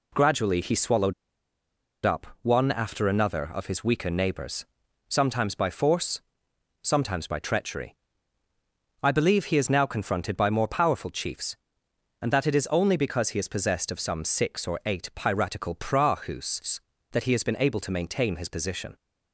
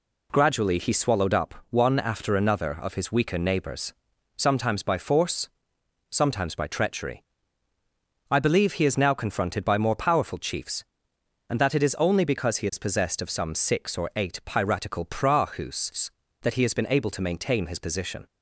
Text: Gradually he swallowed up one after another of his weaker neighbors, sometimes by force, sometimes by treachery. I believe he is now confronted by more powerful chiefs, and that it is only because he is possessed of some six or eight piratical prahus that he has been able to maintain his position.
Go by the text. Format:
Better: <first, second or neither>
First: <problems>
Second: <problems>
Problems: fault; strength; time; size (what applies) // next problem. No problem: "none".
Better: second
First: pauses between "swallowed" and "up"; noticeable; at 1.1 s; 0.91 s long // pauses between "up" and "one"; slight; at 2.2 s; 0.16 s long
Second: pauses between "up" and "one"; slight; at 1.5 s; 0.16 s long